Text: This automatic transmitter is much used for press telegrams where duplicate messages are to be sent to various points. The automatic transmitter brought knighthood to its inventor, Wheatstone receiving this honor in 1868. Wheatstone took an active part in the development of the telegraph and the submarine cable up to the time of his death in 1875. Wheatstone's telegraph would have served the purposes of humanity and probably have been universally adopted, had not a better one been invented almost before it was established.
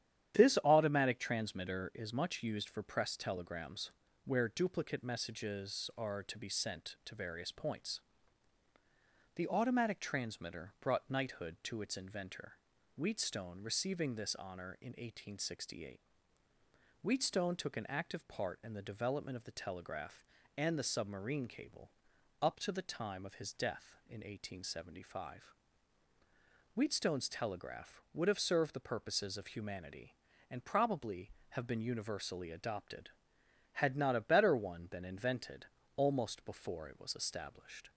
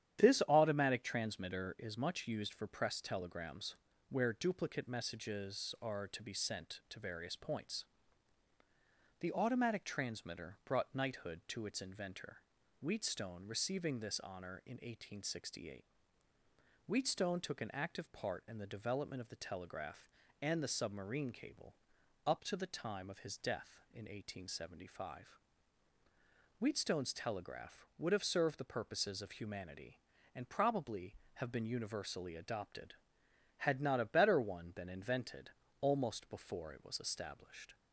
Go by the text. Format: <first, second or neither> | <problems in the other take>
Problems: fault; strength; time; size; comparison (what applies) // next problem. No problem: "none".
neither | starts louder than the rest; strong; the same in both // pauses between "telegrams" and "where"; slight; the same in both // pauses between "cable" and "up"; noticeable; the same in both // pauses between "invented" and "almost"; slight; the same in both